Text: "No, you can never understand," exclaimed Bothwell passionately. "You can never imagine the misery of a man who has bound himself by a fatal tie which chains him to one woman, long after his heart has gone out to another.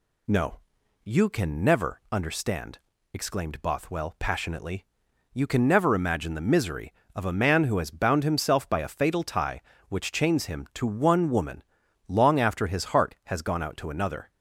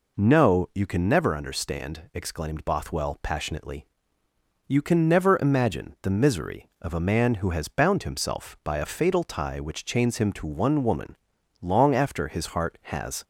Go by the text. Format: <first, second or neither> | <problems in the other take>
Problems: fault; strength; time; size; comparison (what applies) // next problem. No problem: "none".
first | stops before "gone out to another"; at 13.2 s